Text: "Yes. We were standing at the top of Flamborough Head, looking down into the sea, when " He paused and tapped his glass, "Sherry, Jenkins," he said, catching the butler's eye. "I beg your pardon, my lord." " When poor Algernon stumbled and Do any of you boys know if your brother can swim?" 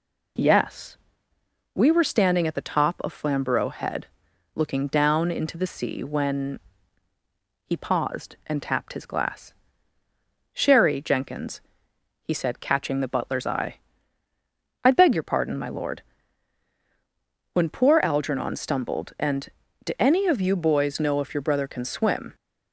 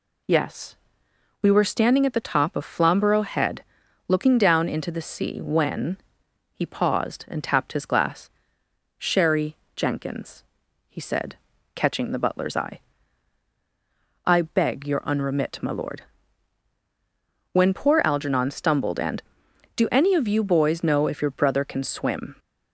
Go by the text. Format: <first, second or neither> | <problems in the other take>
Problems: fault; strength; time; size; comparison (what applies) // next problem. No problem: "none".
first | says "unremit" for "pardon"; at 15.0 s